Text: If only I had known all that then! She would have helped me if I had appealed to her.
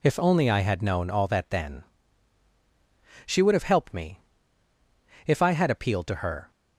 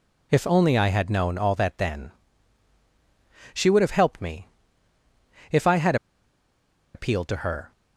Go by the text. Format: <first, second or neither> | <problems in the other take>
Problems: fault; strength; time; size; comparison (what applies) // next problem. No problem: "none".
first | pauses between "me" and "if"; at 4.4 s; 1.0 s long; also in the first // pauses between "had" and "appealed"; at 5.9 s; 0.99 s long